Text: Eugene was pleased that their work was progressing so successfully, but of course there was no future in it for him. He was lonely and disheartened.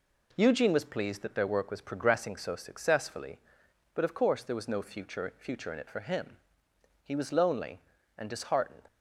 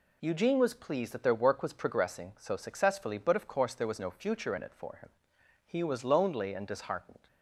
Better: second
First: says "future" twice; at 5.3 s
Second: none

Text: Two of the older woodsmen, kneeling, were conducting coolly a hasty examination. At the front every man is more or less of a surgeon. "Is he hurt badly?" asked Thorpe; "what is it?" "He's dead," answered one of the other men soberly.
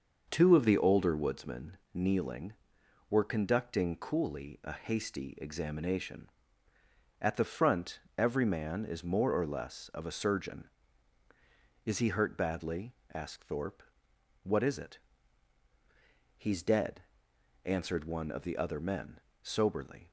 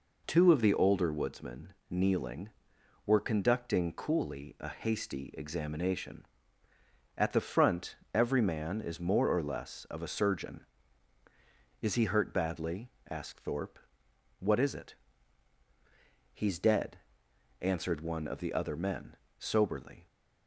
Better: second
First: starts louder than the rest; until 2.0 s; 6.5 dB // pauses between "front" and "every"; slight; at 7.9 s; 0.18 s long // pauses between "men" and "soberly"; slight; at 19.1 s; 0.22 s long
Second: pauses between "front" and "every"; slight; at 7.9 s; 0.18 s long // pauses between "men" and "soberly"; slight; at 19.1 s; 0.22 s long

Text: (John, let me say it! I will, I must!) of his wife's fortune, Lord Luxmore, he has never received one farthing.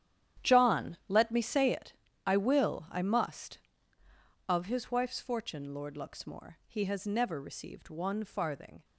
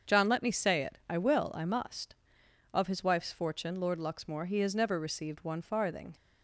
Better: second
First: gets quieter; strong; throughout; 14 dB // starts louder than the rest; strong; until 1.5 s; 10.5 dB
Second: starts louder than the rest; until 1.1 s; 7 dB

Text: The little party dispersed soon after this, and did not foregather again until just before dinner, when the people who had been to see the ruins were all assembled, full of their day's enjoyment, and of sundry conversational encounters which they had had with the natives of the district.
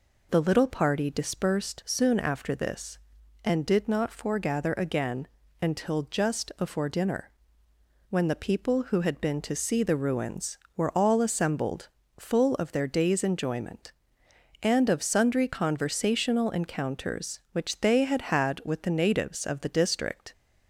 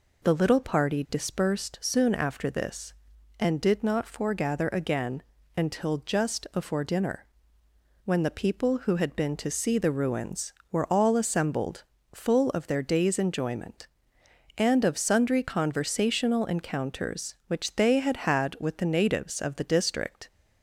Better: neither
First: pauses between "again" and "until"; slight; at 5.2 s; 0.34 s long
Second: pauses between "again" and "until"; slight; at 5.2 s; 0.34 s long

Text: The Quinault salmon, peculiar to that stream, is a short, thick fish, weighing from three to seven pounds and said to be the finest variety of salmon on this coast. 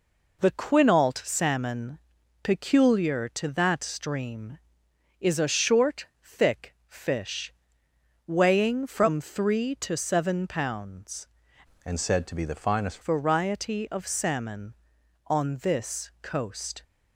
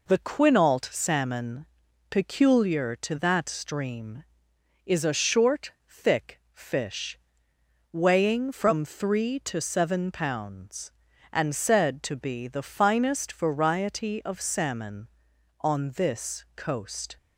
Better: second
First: changes voice from "and" to "finest"; from 11.8 to 12.9 s; 1.1 s long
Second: none

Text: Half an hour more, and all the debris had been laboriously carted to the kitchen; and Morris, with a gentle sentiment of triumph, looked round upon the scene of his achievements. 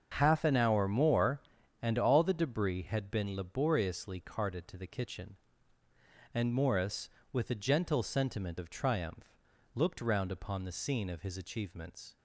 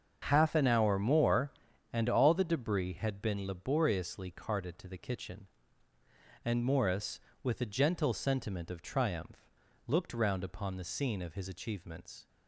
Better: neither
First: starts louder than the rest; until 1.1 s; 6.5 dB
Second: starts louder than the rest; until 1.2 s; 7 dB

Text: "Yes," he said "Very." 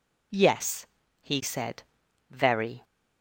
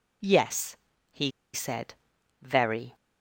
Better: first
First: pauses between "said" and "Very"; noticeable; at 1.8 s; 0.46 s long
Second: pauses between "he" and "said"; slight; at 1.3 s; 0.23 s long // pauses between "said" and "Very"; noticeable; at 1.9 s; 0.46 s long

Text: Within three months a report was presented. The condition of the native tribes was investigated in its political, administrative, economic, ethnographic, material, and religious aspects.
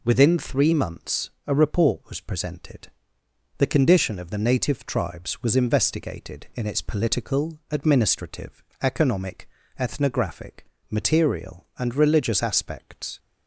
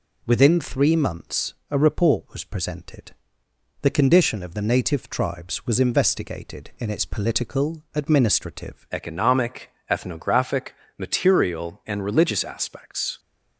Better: first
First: none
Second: changes voice at "economic"; from 8.9 s on; 4.2 s long

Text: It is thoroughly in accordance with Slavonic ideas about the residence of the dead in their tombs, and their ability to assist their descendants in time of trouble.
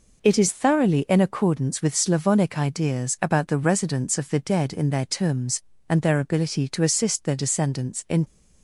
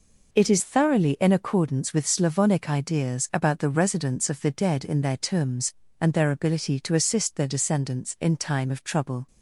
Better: second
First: stops before "time of trouble"; at 8.2 s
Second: none

